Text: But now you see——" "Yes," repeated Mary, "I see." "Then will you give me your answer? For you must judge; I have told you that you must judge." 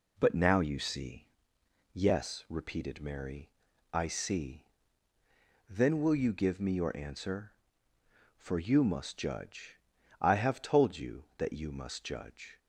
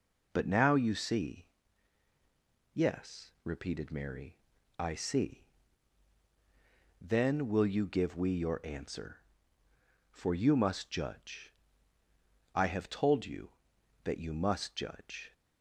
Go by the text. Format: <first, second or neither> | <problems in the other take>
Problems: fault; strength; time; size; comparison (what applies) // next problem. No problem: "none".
first | says "we" for "me"; at 8.1 s